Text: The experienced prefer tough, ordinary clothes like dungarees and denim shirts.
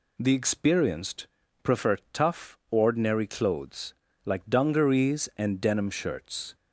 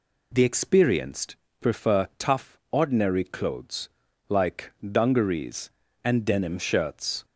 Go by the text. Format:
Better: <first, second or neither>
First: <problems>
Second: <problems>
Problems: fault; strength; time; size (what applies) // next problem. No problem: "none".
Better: neither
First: pauses between "experienced" and "prefer"; slight; at 1.2 s; 0.34 s long // pauses between "clothes" and "like"; slight; at 3.9 s; 0.32 s long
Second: pauses between "experienced" and "prefer"; slight; at 1.3 s; 0.24 s long // pauses between "clothes" and "like"; at 3.9 s; 0.40 s long